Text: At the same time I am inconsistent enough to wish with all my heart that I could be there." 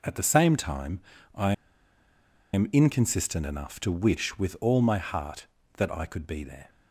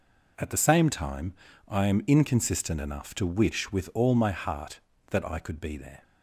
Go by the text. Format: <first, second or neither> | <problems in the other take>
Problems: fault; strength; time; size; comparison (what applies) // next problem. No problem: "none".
second | pauses between "time" and "I"; slight; at 1.0 s; 0.34 s long; slight in the second // pauses between "I" and "am"; at 1.5 s; 1.0 s long